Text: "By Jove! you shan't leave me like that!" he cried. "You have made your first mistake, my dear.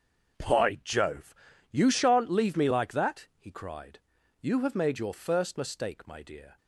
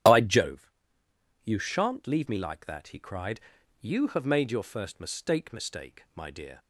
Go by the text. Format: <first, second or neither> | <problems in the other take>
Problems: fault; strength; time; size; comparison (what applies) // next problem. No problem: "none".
first | starts louder than the rest; strong; until 1.7 s; 10 dB; also in the first // says "mistake" twice; at 5.5 s